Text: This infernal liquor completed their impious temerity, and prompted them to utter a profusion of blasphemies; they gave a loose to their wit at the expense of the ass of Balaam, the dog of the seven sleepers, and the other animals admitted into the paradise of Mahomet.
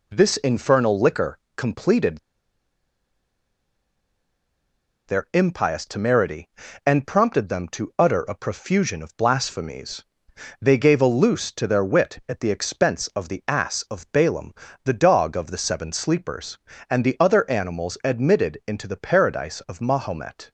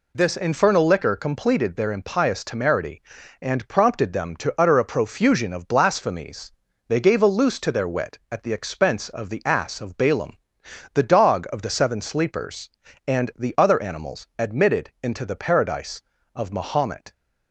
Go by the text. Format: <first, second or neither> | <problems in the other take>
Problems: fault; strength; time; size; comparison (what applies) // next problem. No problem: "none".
second | pauses between "liquor" and "completed"; slight; at 1.3 s; 0.20 s long // pauses between "completed" and "their"; strong; at 2.1 s; 2.8 s long